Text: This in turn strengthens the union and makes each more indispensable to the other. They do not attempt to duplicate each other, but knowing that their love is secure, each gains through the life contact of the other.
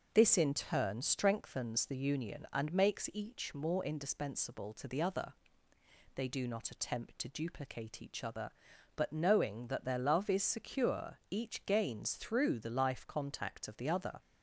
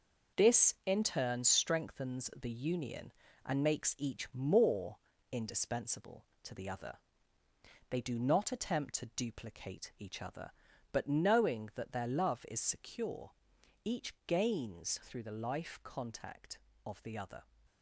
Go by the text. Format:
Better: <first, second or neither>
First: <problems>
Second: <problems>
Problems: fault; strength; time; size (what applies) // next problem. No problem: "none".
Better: first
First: none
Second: gets quieter; strong; throughout; 7.5 dB // pauses between "more" and "indispensable"; slight; at 4.9 s; 0.34 s long